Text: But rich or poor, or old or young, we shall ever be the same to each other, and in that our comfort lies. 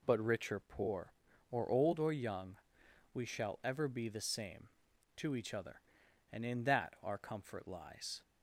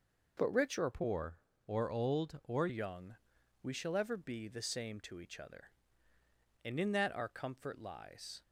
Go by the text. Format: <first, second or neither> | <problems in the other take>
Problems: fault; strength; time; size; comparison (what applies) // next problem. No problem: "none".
first | changes voice from "poor" to "or"; from 0.9 to 2.6 s; 1.7 s long